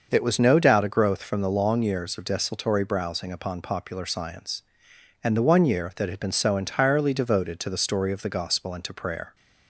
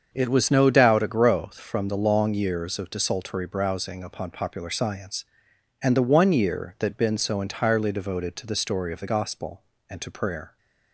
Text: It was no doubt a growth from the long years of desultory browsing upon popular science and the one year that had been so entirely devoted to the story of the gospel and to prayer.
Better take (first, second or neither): first